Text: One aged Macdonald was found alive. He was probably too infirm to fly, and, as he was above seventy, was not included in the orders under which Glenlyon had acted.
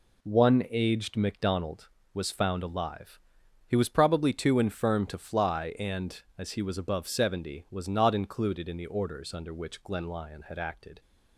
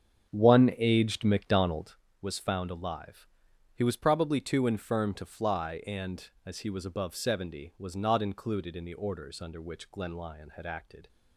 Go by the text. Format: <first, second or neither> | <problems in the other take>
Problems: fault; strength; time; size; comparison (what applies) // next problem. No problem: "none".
first | starts louder than the rest; strong; until 2.0 s; 7.5 dB